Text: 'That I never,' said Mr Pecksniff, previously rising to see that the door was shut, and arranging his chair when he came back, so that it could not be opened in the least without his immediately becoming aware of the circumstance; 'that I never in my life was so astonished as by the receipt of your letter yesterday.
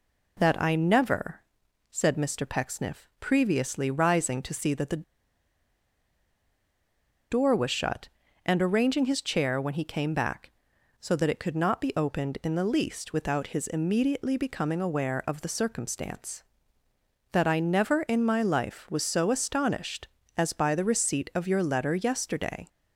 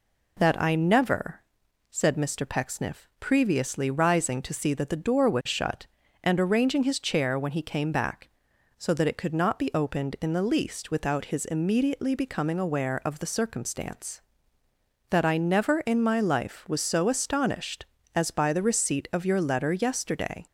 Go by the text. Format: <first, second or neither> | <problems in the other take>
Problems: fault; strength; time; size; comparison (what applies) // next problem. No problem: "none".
second | pauses between "the" and "door"; strong; at 5.0 s; 2.2 s long